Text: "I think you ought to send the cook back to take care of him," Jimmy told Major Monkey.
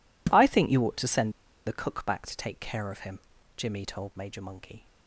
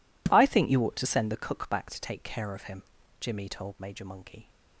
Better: second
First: pauses between "send" and "the"; slight; at 1.3 s; 0.34 s long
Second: none

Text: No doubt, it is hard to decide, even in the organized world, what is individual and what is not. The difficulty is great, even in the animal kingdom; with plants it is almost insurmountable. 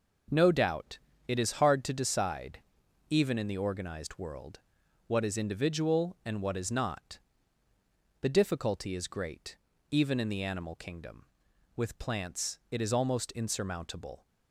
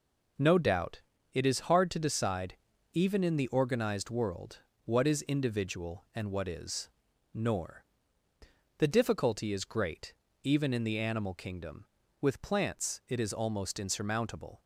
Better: first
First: none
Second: says "nor" for "not"; at 7.3 s

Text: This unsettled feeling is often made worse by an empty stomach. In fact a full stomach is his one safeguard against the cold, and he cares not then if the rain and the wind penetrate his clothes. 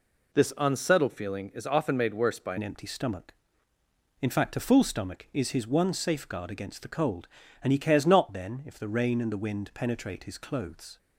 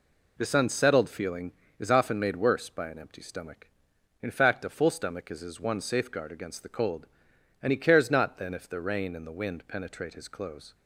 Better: second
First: changes voice at "an"; from 2.5 s on; 8.4 s long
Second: none

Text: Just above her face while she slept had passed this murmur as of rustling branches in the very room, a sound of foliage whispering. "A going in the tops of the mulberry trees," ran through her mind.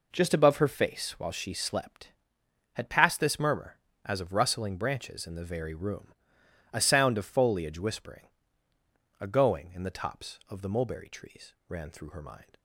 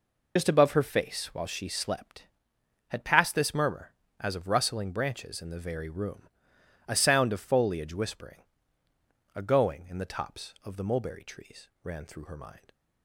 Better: first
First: none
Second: loses the start of "Just"; at 0.3 s; 90 ms

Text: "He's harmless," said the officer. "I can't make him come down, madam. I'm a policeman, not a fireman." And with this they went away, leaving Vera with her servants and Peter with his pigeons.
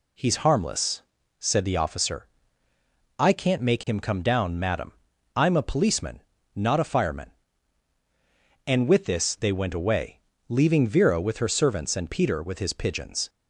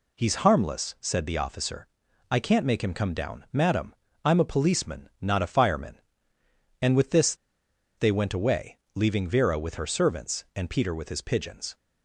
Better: first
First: none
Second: pauses between "this" and "they"; noticeable; at 7.3 s; 0.63 s long

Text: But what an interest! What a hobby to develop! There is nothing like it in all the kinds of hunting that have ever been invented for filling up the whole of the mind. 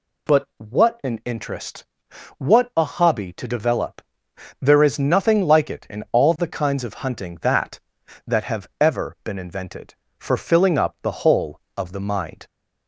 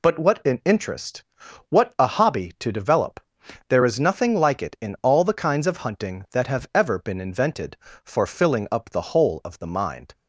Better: second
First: says "that" twice; at 8.2 s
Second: none

